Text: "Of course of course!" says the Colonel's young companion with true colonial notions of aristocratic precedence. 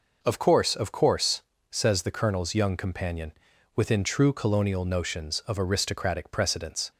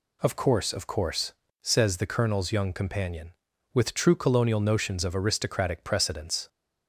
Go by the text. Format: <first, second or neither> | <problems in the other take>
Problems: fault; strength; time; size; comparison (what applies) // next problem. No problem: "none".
second | says "within" for "with"; at 3.7 s